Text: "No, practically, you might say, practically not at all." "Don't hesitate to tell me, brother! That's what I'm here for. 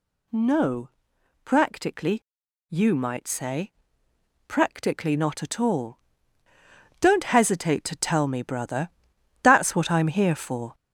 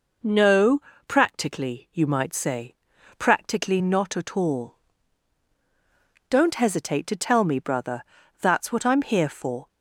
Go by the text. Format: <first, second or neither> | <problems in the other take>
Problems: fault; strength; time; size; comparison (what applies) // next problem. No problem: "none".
second | gets louder; noticeable; throughout; 5.5 dB